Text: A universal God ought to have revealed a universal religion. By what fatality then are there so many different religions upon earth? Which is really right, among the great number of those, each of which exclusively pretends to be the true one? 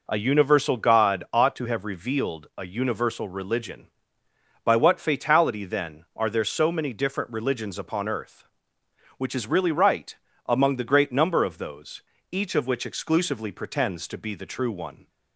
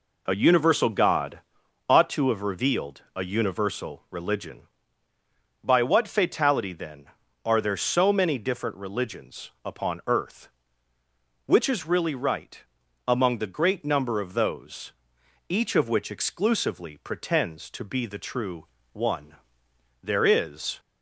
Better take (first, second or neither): first